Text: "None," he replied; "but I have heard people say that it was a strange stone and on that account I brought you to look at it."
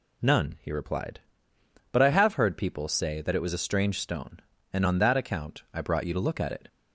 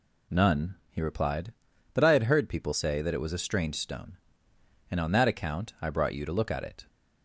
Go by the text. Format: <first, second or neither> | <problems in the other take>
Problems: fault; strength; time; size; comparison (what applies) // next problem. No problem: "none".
first | says "had" for "have"; at 2.1 s